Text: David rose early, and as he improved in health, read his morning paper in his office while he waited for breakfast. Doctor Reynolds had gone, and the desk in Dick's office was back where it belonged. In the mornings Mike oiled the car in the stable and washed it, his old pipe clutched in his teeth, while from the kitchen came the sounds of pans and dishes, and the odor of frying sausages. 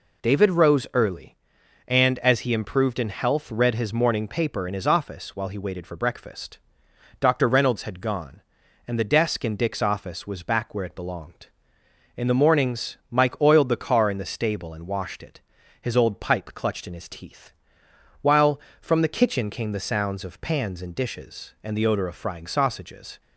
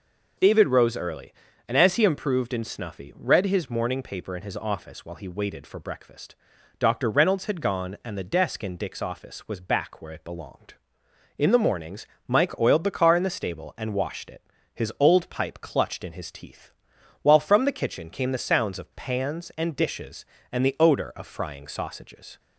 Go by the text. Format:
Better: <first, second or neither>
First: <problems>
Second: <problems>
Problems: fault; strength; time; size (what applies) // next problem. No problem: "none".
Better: first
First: none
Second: says "snuffy" for "health"; at 2.6 s // pauses between "mornings" and "Mike"; slight; at 12.0 s; 0.22 s long